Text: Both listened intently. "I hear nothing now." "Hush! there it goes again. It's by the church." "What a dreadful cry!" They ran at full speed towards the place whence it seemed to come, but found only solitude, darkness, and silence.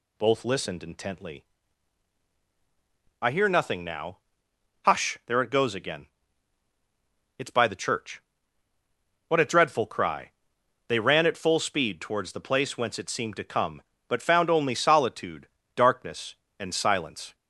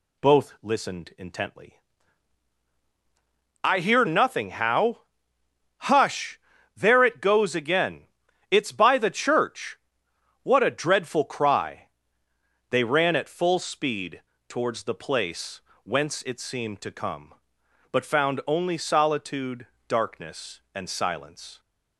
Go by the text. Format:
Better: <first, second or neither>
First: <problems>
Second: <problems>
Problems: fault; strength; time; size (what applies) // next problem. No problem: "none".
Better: first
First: none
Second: says "how" for "now"; at 4.4 s // pauses between "speed" and "towards"; slight; at 14.2 s; 0.26 s long // pauses between "place" and "whence"; slight; at 15.5 s; 0.24 s long